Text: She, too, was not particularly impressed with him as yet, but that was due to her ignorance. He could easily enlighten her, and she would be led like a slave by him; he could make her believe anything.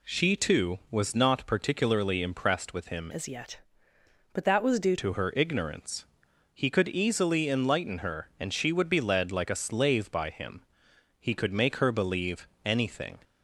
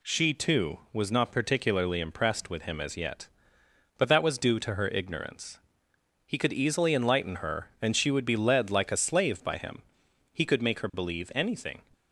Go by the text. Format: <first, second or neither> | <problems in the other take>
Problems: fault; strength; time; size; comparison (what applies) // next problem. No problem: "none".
second | changes voice from "as" to "due"; from 3.1 to 4.9 s; 1.8 s long // pauses between "believe" and "anything"; slight; at 12.4 s; 0.18 s long